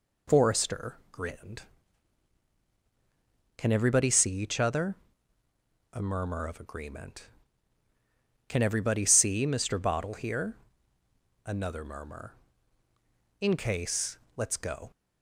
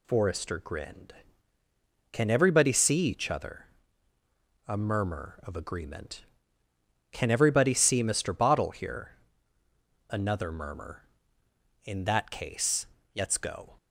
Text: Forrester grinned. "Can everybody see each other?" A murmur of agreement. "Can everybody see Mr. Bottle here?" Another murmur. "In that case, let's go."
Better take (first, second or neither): second